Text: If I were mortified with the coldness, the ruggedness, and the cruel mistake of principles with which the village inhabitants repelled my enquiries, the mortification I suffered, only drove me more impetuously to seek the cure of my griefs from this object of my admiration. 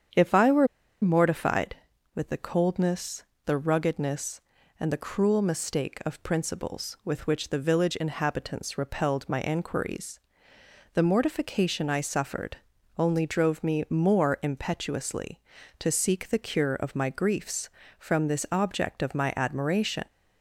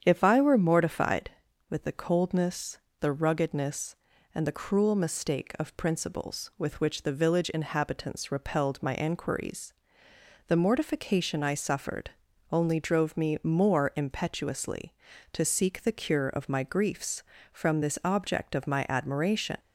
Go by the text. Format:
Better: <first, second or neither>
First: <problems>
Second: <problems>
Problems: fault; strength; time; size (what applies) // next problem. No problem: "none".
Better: second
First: starts louder than the rest; strong; until 1.5 s; 8.5 dB // pauses between "were" and "mortified"; slight; at 0.6 s; 0.35 s long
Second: starts louder than the rest; strong; until 1.0 s; 8.5 dB